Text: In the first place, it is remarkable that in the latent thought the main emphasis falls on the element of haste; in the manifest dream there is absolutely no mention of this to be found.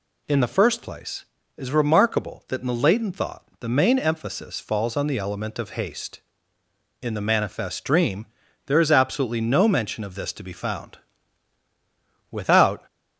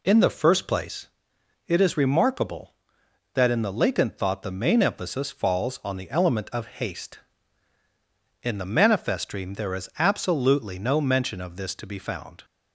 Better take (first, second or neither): second